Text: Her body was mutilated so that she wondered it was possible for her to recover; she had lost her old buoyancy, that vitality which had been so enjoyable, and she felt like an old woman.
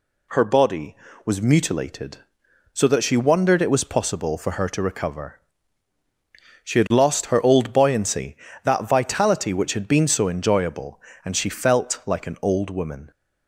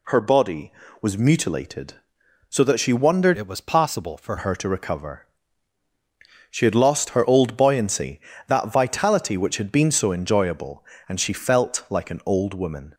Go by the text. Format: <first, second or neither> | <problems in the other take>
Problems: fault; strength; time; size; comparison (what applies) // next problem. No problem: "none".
first | changes voice from "it" to "for"; from 3.3 to 4.3 s; 1.0 s long